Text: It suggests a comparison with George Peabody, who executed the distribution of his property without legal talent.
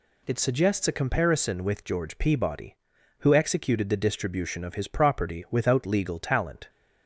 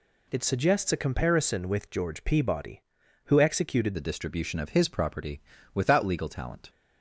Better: first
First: none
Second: changes voice at "the"; from 3.9 s on; 2.7 s long // pauses between "property" and "without"; slight; at 5.4 s; 0.32 s long

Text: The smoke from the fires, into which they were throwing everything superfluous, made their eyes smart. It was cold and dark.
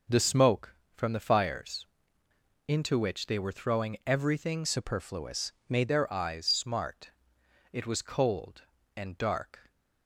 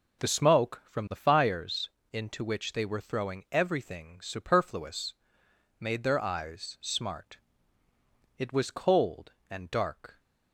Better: second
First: changes voice from "superfluous" to "made"; from 4.6 to 5.9 s; 1.3 s long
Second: none

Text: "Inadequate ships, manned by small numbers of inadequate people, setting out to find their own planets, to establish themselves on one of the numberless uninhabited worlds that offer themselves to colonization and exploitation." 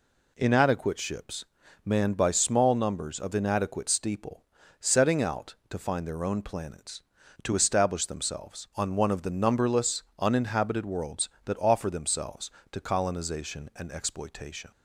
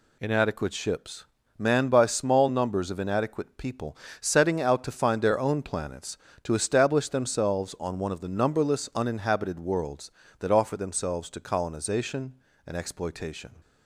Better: second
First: says "steeple" for "people"; at 3.8 s // pauses between "numberless" and "uninhabited"; slight; at 10.0 s; 0.16 s long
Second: none

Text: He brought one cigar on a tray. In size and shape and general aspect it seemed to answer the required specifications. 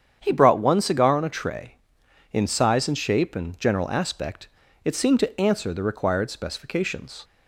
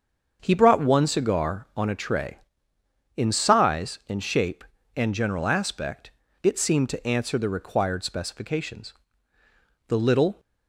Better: first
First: starts louder than the rest; strong; until 1.2 s; 8.5 dB // pauses between "aspect" and "it"; slight; at 4.4 s; 0.36 s long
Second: starts louder than the rest; until 1.4 s; 7 dB // pauses between "aspect" and "it"; slight; at 6.0 s; 0.32 s long // goes on to say "The little"; from 9.8 s on; 0.52 s long

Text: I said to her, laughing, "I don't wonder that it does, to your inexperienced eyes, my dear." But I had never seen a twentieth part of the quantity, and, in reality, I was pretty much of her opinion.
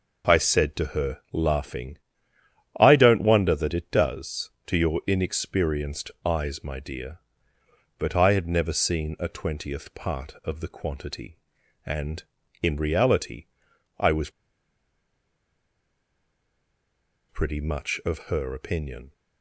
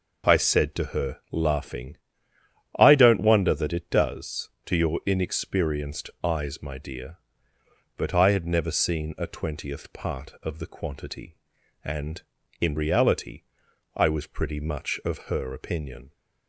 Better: second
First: pauses between "was" and "pretty"; strong; at 14.2 s; 2.9 s long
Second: none

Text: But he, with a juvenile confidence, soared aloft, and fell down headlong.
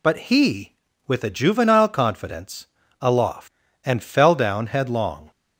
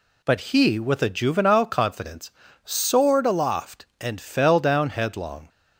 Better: second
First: skips "soared"; at 2.8 s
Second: none

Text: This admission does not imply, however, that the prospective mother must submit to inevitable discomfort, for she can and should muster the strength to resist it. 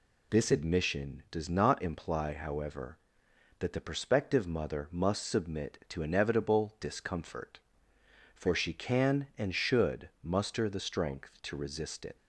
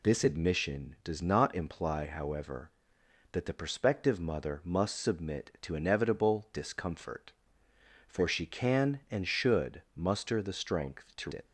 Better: first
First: none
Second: skips "resist"; at 11.3 s

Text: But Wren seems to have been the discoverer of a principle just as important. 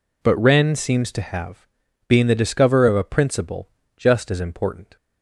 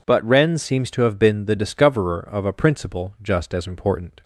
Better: second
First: says "being" for "been"; at 2.0 s // pauses between "principle" and "just"; slight; at 3.6 s; 0.28 s long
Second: none

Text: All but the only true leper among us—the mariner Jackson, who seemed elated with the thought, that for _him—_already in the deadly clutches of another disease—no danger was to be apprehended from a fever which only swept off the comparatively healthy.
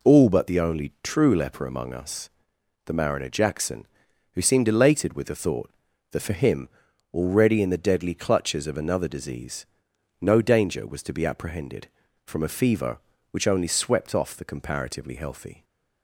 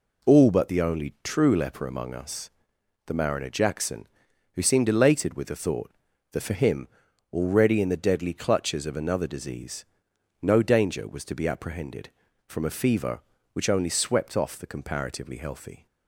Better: neither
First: none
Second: none

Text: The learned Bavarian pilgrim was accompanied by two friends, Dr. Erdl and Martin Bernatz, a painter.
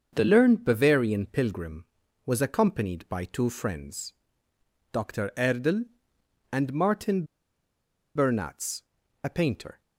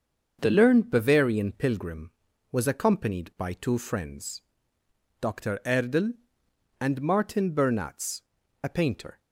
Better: second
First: starts louder than the rest; until 1.1 s; 6.5 dB // pauses between "Martin" and "Bernatz"; noticeable; at 7.2 s; 0.89 s long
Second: starts louder than the rest; until 1.4 s; 6.5 dB

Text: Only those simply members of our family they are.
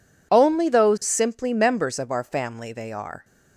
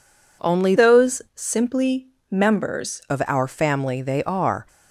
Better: first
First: none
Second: changes voice from "those" to "members"; from 0.7 to 3.0 s; 2.3 s long // pauses between "simply" and "members"; slight; at 2.0 s; 0.24 s long

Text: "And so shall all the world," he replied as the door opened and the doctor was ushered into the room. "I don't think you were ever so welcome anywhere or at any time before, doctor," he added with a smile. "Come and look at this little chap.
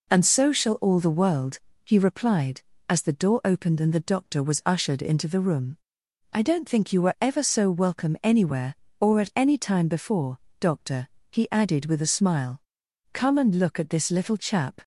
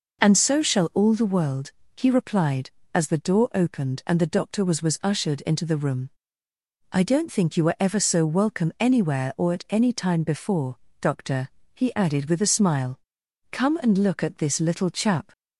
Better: first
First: none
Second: says "was" twice; at 4.8 s

